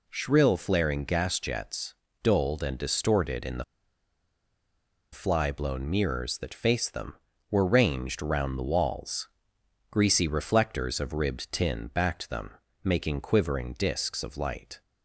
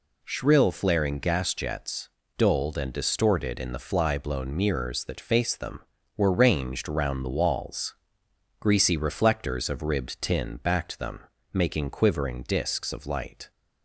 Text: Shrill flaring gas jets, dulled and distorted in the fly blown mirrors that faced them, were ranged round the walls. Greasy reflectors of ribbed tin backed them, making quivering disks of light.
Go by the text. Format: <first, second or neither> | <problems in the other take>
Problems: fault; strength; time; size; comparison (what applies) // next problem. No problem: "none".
second | pauses between "the" and "fly"; strong; at 3.6 s; 1.4 s long